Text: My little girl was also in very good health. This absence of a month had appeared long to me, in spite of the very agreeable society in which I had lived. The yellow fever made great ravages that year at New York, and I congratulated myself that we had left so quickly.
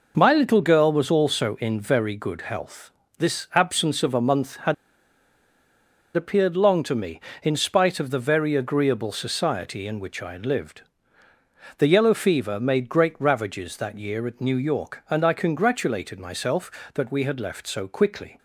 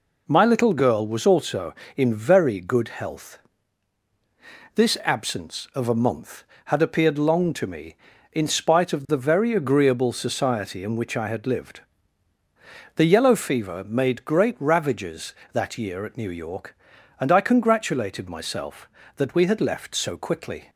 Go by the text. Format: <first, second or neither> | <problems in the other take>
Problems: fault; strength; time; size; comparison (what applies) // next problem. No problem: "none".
second | pauses between "had" and "appeared"; strong; at 4.7 s; 1.4 s long